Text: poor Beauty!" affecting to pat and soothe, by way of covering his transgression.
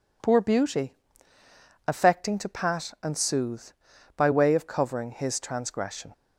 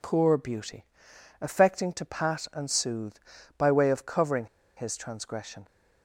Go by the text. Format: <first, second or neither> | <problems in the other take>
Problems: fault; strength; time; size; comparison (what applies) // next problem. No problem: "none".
first | pauses between "covering" and "his"; slight; at 4.4 s; 0.30 s long